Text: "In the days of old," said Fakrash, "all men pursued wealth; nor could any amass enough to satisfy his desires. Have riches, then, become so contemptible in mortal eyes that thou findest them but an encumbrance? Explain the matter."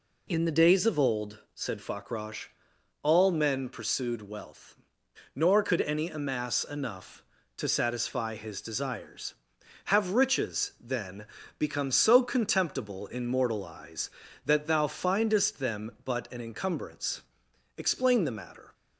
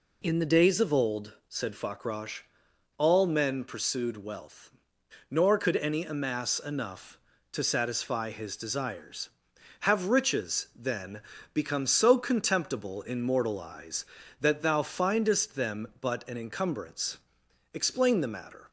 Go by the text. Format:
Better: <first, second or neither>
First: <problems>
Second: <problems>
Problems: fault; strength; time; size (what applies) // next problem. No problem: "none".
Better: neither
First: none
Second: none